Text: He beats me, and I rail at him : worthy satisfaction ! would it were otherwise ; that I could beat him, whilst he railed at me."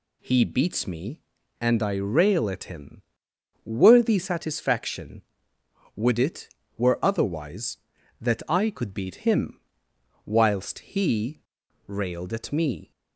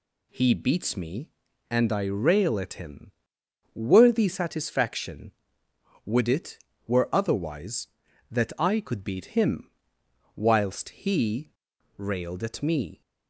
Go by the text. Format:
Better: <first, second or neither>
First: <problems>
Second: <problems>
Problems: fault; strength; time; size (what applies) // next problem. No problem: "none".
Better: neither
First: pauses between "he" and "railed"; noticeable; at 11.3 s; 0.48 s long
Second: pauses between "he" and "railed"; noticeable; at 11.4 s; 0.48 s long